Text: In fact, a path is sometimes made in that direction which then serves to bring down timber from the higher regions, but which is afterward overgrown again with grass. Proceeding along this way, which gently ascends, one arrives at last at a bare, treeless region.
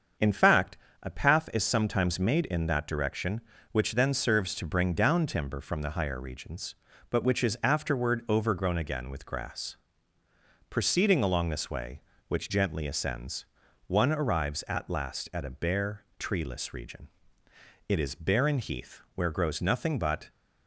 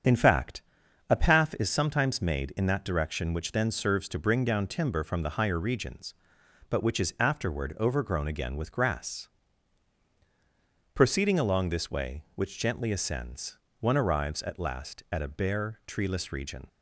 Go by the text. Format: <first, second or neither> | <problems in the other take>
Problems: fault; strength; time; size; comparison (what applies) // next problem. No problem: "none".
second | starts louder than the rest; until 1.4 s; 7 dB; strong in the second // goes on to say "It is barren heath where grows nothing but"; strong; from 17.8 s on; 2.4 s long